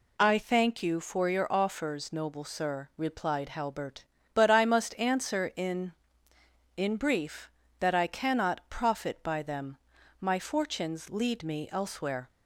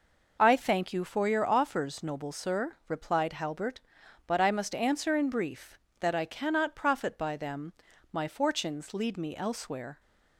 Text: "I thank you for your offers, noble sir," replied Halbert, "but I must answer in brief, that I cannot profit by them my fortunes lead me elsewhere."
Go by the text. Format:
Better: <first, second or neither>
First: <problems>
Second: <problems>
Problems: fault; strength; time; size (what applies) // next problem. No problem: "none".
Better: second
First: says "in" twice; at 6.7 s // pauses between "them" and "my"; at 9.7 s; 0.44 s long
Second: pauses between "them" and "my"; at 7.7 s; 0.40 s long